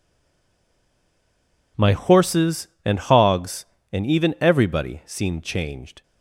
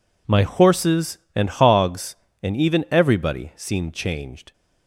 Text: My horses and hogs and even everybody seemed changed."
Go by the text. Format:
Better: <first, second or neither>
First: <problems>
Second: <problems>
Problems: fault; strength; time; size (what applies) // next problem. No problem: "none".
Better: second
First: stays silent before the first word; noticeable; until 1.7 s; 1.7 s long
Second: none